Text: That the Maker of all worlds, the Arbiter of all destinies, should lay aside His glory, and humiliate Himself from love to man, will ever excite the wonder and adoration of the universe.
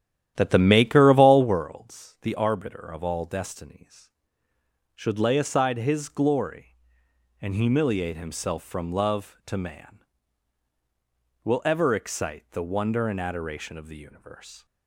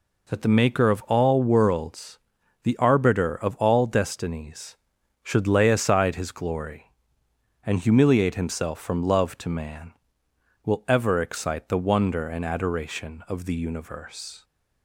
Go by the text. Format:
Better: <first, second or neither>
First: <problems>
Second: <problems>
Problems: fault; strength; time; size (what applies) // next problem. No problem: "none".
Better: second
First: starts louder than the rest; strong; until 1.7 s; 11.5 dB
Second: none